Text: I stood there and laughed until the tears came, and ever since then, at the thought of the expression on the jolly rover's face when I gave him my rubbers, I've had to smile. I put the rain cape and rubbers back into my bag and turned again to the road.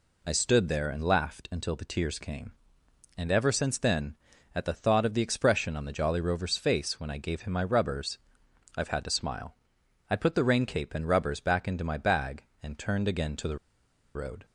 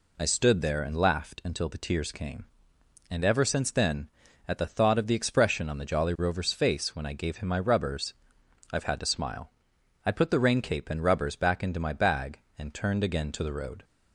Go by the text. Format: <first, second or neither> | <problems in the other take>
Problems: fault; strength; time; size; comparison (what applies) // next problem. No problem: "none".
second | pauses between "the" and "road"; noticeable; at 13.5 s; 0.59 s long